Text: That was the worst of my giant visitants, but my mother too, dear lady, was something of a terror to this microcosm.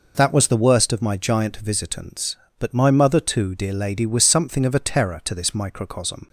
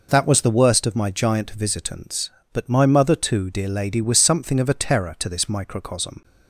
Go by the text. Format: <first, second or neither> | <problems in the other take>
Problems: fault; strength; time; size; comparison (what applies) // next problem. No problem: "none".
neither | none